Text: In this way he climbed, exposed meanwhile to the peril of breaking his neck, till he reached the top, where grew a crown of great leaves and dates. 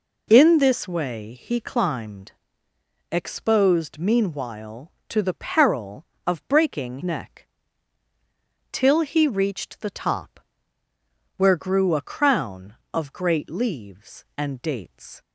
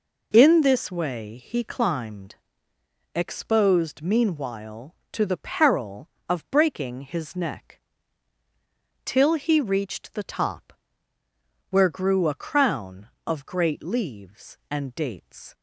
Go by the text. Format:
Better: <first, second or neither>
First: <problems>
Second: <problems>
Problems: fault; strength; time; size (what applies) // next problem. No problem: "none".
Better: second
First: skips "his"; at 7.0 s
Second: none